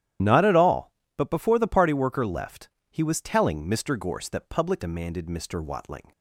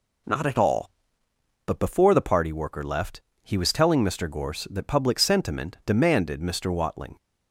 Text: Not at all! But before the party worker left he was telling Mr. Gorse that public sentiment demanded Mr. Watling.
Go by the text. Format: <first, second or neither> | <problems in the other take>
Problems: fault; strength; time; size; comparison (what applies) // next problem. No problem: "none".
second | starts louder than the rest; strong; until 1.4 s; 11.5 dB // pauses between "left" and "he"; slight; at 2.6 s; 0.22 s long; slight in the second // skips "sentiment"; at 4.8 s